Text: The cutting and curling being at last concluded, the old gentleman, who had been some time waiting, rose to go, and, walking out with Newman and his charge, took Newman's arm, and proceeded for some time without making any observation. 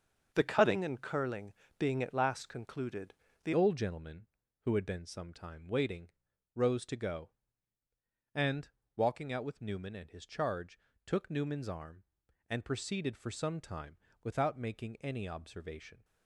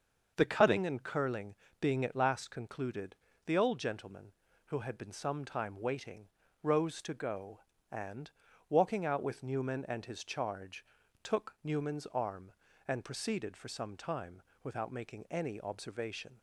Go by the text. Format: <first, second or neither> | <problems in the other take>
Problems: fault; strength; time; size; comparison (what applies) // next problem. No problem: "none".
second | starts louder than the rest; until 1.3 s; 6.5 dB; also in the second // pauses between "curling" and "being"; slight; at 1.5 s; 0.24 s long; slight in the second // changes voice at "old"; from 3.5 s on; 12.5 s long // pauses between "time" and "without"; slight; at 13.9 s; 0.26 s long; slight in the second